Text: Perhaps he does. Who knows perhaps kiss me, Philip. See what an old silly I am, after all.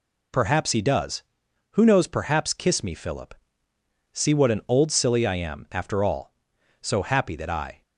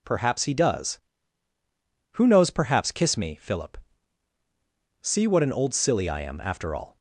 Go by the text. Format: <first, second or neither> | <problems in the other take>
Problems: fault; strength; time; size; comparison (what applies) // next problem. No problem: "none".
second | goes on to say "So happy that I"; noticeable; from 6.8 s on; 1.0 s long